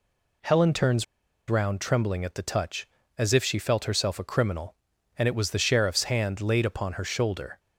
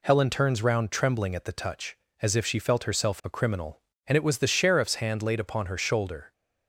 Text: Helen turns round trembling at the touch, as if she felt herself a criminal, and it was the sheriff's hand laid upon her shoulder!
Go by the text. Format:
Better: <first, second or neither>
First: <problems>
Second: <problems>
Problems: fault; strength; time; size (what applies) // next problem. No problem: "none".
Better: second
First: pauses between "turns" and "round"; at 1.0 s; 0.43 s long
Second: none